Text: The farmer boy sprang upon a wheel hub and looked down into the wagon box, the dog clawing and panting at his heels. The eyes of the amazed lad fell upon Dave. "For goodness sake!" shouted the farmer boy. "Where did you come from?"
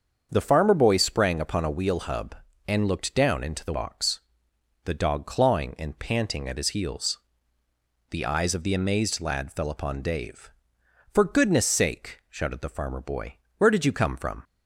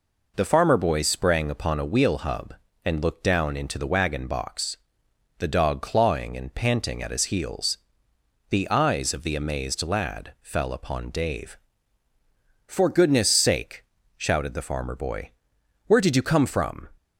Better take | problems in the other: second | starts louder than the rest; until 1.3 s; 7 dB // skips "wagon"; at 3.7 s

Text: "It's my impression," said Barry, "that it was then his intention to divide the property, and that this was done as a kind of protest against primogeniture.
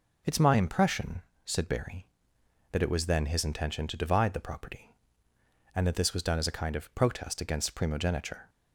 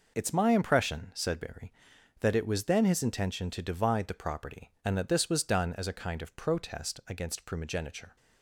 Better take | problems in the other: first | gets quieter; strong; throughout; 8.5 dB

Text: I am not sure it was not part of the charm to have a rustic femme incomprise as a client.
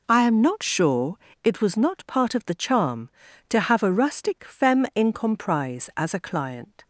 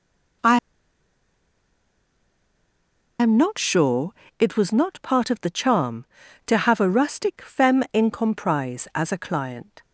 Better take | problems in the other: first | pauses between "I" and "am"; strong; at 0.5 s; 2.6 s long // pauses between "sure" and "it"; slight; at 4.1 s; 0.28 s long; slight in the first

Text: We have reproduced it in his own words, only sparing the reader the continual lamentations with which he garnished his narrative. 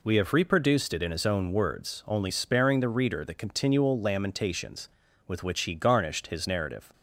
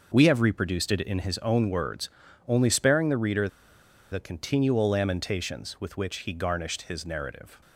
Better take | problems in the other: first | pauses between "reader" and "the"; noticeable; at 3.4 s; 0.62 s long

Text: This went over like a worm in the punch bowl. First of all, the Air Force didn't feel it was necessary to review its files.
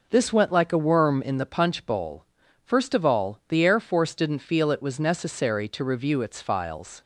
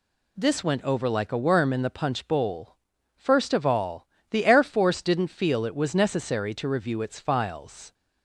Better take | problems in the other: second | skips "over"; at 0.5 s

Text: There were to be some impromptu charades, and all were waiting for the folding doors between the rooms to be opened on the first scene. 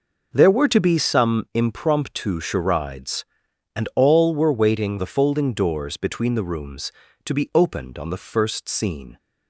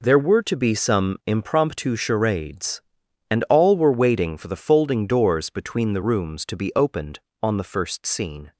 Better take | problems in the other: second | skips "for"; at 4.9 s

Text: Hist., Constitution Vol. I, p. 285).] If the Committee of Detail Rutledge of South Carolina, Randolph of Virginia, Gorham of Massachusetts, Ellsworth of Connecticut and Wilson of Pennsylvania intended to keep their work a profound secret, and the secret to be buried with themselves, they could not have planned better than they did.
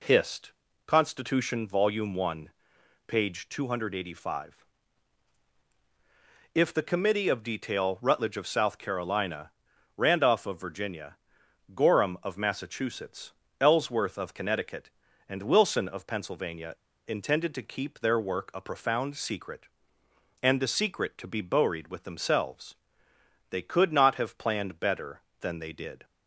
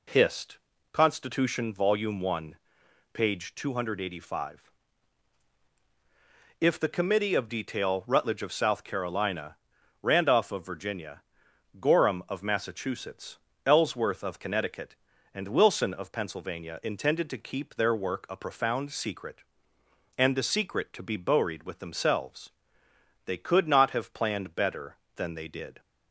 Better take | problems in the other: second | pauses between "Pennsylvania" and "intended"; slight; at 16.7 s; 0.34 s long

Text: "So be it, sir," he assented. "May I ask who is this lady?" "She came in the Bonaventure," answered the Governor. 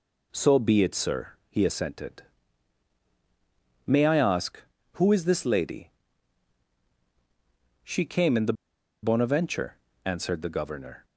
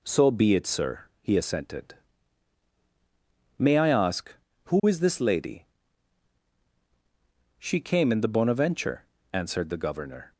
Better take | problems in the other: second | pauses between "the" and "Bonaventure"; noticeable; at 8.5 s; 0.49 s long

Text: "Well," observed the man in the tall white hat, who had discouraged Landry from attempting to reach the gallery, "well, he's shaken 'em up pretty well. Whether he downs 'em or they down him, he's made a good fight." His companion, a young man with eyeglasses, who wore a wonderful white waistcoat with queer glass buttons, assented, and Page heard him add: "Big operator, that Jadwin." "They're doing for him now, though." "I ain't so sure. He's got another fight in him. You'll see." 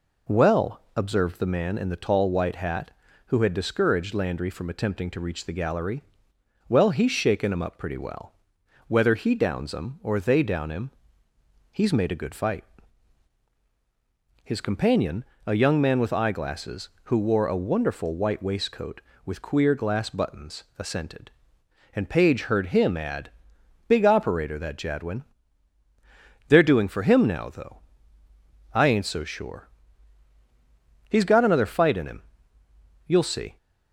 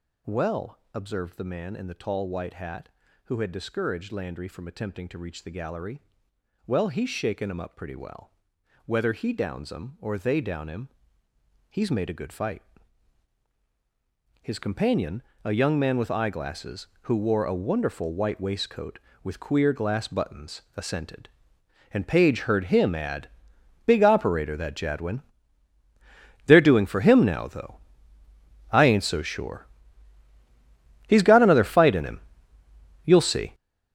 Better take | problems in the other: first | gets louder; strong; throughout; 12.5 dB

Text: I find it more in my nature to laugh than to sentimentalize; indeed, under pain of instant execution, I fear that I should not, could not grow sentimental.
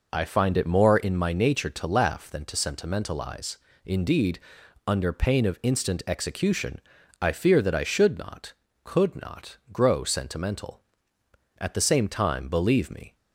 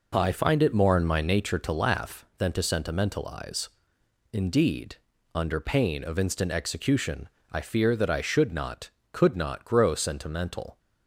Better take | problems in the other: second | pauses between "not" and "grow"; slight; at 9.5 s; 0.16 s long // goes on to say "At the same time believe me"; from 11.5 s on; 1.5 s long

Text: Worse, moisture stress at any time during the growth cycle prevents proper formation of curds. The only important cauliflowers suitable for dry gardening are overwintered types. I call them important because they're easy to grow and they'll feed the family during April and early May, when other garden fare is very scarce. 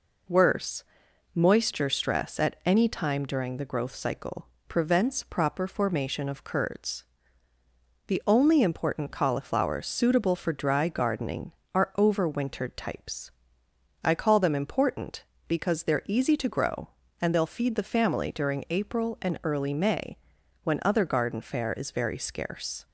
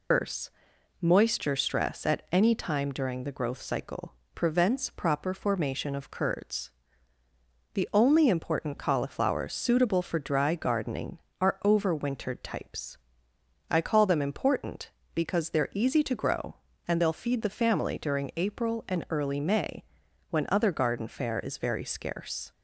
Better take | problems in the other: first | loses the start of "Worse"; at 0.1 s; 155 ms // pauses between "cycle" and "prevents"; slight; at 4.1 s; 0.22 s long; slight in the first

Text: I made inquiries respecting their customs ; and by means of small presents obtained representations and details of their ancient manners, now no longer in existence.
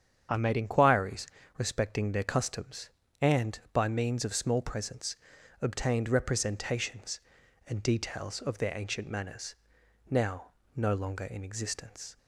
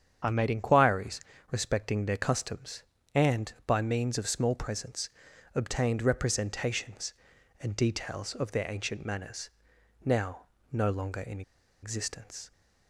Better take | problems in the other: first | starts louder than the rest; strong; until 1.5 s; 8 dB; strong in the first // pauses between "inquiries" and "respecting"; slight; at 1.1 s; 0.32 s long; slight in the first // pauses between "presents" and "obtained"; at 5.0 s; 0.44 s long; also in the first // pauses between "now" and "no"; slight; at 10.4 s; 0.28 s long; slight in the first // pauses between "in" and "existence"; at 11.4 s; 0.41 s long

